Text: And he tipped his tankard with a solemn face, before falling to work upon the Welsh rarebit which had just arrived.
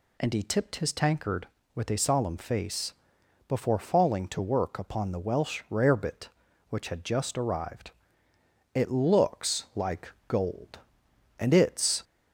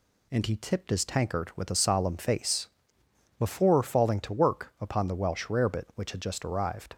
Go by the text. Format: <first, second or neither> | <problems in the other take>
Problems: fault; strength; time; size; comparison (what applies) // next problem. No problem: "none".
second | goes on to say "It looks like gold and it's"; strong; from 8.7 s on; 3.3 s long